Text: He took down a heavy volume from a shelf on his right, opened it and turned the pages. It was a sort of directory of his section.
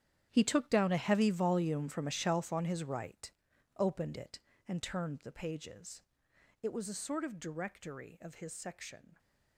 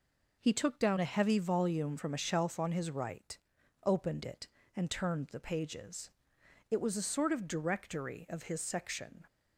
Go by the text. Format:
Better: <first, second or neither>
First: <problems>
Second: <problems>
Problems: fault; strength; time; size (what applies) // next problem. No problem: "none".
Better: second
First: gets quieter; strong; throughout; 14.5 dB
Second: none